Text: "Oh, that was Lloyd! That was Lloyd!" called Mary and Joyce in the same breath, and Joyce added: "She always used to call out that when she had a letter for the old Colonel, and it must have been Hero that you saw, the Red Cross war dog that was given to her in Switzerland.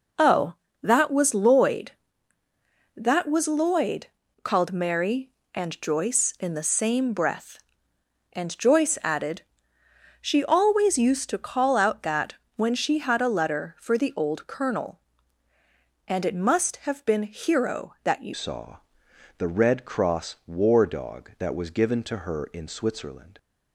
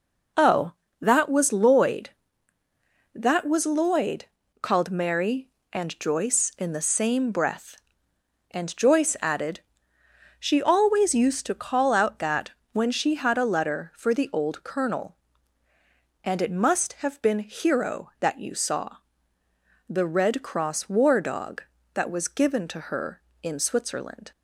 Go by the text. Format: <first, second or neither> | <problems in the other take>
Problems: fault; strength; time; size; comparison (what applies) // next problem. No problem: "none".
second | pauses between "that" and "when"; slight; at 12.3 s; 0.20 s long; slight in the second // changes voice at "saw"; from 18.3 s on; 5.0 s long